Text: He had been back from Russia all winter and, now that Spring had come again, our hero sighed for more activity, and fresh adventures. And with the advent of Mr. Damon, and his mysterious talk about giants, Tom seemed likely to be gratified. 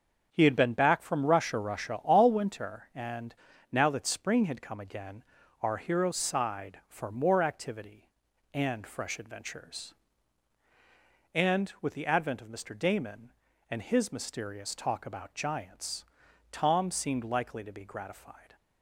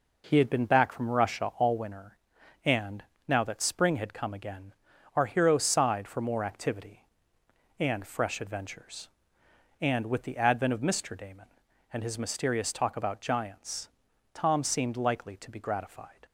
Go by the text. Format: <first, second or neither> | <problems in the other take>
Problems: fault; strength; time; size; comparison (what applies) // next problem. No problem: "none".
second | starts louder than the rest; until 1.3 s; 6.5 dB // says "Russia" twice; at 1.5 s